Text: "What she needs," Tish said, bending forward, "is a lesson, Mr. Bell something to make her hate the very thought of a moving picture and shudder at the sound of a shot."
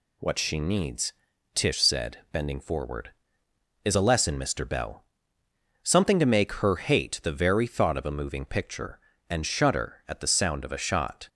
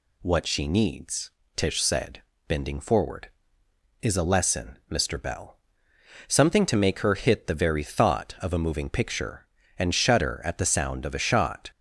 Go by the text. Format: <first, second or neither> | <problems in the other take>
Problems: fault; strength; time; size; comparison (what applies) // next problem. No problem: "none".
first | pauses between "Bell" and "something"; noticeable; at 5.5 s; 0.74 s long; noticeable in the first // says "hit" for "hate"; at 7.1 s